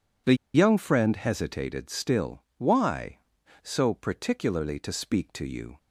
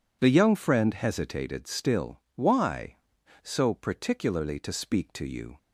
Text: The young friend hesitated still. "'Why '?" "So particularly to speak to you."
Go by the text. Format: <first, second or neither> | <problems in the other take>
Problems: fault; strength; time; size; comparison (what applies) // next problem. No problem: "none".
second | pauses between "The" and "young"; slight; at 0.3 s; 0.20 s long